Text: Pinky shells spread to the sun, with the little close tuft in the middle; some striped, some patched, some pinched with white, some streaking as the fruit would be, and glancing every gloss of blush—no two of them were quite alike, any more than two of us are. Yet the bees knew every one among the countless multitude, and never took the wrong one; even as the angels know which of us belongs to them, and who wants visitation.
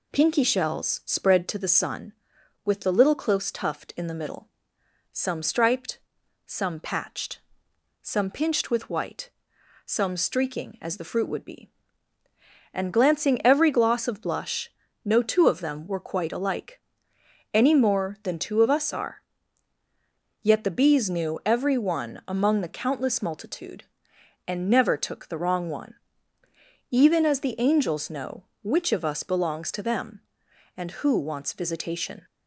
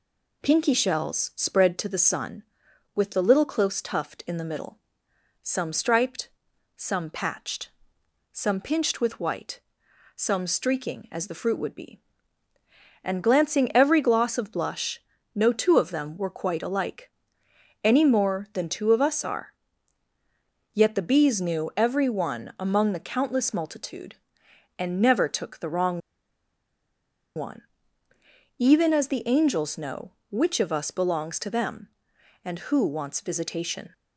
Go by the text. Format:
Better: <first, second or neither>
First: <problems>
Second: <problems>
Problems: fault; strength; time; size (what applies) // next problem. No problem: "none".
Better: first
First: none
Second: pauses between "wrong" and "one"; strong; at 25.9 s; 1.3 s long